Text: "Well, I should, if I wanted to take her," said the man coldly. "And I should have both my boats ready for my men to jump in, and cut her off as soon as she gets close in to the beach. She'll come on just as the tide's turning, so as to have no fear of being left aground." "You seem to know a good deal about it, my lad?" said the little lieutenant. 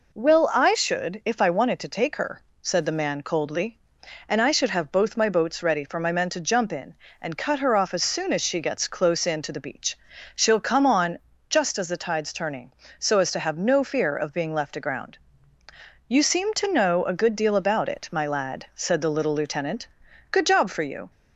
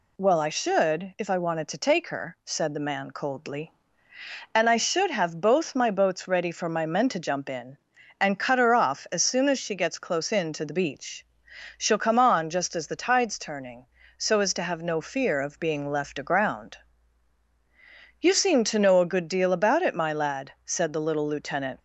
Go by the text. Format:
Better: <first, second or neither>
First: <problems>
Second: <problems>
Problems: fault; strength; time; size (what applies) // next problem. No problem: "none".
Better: second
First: pauses between "on" and "just"; slight; at 11.2 s; 0.28 s long // goes on to say "Good job for you"; noticeable; from 20.3 s on; 0.78 s long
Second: none